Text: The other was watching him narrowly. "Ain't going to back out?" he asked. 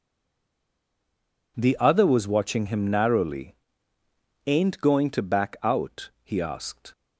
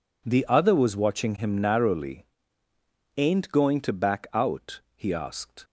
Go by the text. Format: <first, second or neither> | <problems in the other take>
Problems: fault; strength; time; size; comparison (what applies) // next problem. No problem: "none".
second | stays silent before the first word; noticeable; until 1.5 s; 1.5 s long